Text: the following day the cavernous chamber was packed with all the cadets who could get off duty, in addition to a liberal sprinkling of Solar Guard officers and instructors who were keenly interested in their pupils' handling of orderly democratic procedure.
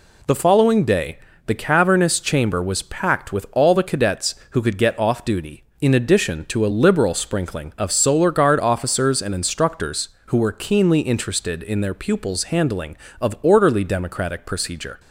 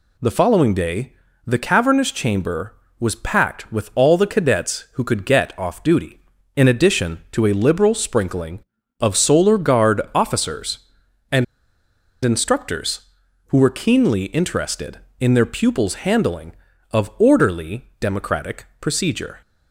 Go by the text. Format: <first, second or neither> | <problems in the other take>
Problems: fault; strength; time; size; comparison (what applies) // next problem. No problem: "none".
first | pauses between "day" and "the"; slight; at 1.1 s; 0.32 s long; slight in the first // pauses between "and" and "instructors"; noticeable; at 11.4 s; 0.80 s long